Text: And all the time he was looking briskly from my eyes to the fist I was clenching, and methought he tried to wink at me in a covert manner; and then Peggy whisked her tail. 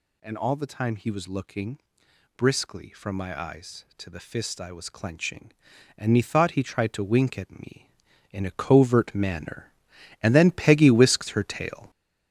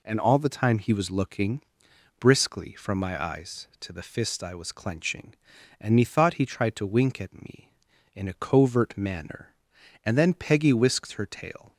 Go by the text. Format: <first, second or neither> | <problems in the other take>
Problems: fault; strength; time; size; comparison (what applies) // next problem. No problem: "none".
second | gets louder; throughout; 7 dB // pauses between "looking" and "briskly"; noticeable; at 1.7 s; 0.58 s long; noticeable in the second